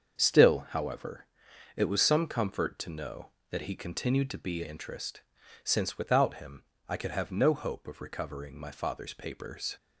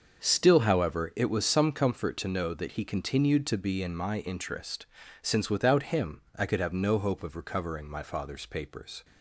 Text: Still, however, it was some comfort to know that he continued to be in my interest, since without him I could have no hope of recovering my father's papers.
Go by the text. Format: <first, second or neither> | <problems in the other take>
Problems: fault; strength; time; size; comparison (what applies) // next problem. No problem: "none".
second | starts louder than the rest; until 1.2 s; 7 dB; also in the second // skips "in my"; at 4.6 s // pauses between "him" and "I"; slight; at 6.6 s; 0.24 s long